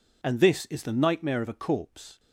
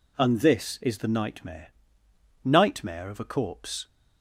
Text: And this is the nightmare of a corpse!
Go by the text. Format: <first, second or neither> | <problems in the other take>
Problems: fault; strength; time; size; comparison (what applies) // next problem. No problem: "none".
first | says "nightmare" twice; at 2.4 s